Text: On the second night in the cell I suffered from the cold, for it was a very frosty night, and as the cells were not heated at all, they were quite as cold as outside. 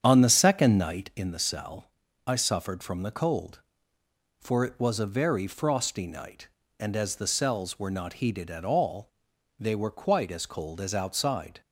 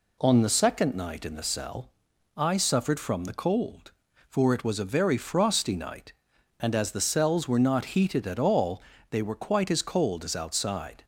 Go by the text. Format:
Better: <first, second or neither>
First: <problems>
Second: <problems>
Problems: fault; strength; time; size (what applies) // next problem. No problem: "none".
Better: second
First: starts louder than the rest; strong; until 1.3 s; 8.5 dB // pauses between "cell" and "I"; slight; at 1.9 s; 0.34 s long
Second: pauses between "cell" and "I"; at 1.9 s; 0.44 s long